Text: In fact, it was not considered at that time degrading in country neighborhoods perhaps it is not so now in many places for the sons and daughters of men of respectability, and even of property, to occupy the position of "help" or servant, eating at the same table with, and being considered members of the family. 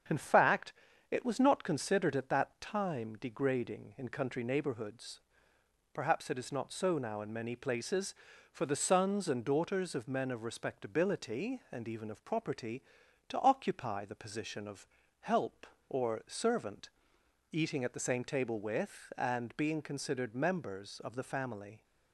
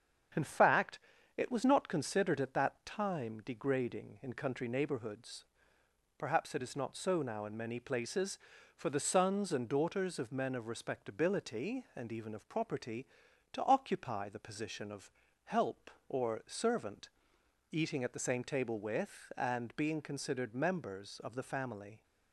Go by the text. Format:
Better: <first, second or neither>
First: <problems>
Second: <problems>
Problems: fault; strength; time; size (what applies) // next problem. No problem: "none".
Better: neither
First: starts louder than the rest; strong; until 1.4 s; 7.5 dB // pauses between "neighborhoods" and "perhaps"; noticeable; at 5.2 s; 0.72 s long // pauses between "of" and "help"; slight; at 14.8 s; 0.34 s long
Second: starts louder than the rest; strong; until 1.7 s; 7.5 dB // pauses between "neighborhoods" and "perhaps"; noticeable; at 5.4 s; 0.72 s long // pauses between "of" and "help"; slight; at 15.1 s; 0.34 s long